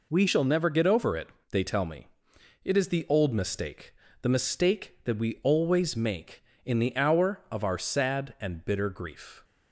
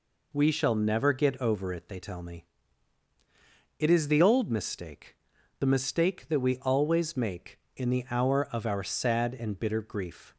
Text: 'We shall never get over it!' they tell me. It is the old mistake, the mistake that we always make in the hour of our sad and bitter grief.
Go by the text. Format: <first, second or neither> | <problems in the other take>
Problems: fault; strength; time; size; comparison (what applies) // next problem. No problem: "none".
second | changes voice at "shall"; from 0.2 s on; 9.2 s long